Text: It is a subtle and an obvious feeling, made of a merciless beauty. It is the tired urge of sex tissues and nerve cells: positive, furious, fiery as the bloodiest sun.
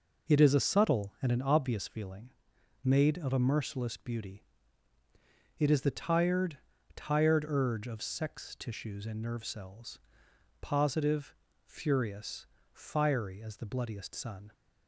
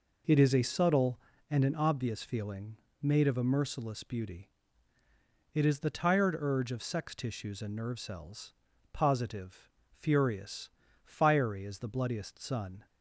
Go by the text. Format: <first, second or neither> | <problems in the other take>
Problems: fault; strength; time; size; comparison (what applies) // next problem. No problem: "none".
second | says "tired" twice; at 6.9 s